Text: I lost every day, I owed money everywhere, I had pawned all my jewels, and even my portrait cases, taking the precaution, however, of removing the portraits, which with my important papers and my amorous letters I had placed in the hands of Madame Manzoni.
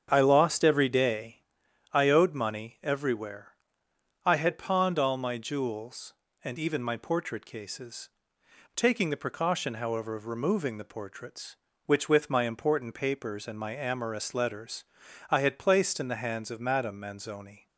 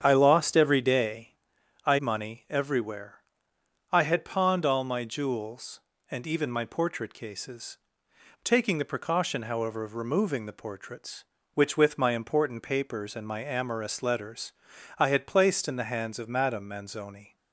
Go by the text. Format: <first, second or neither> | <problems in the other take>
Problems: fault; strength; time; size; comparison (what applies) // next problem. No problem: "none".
first | starts louder than the rest; strong; until 1.0 s; 8 dB; strong in the first // skips "owed"; at 1.9 s // pauses between "letters" and "I"; at 14.5 s; 0.44 s long; also in the first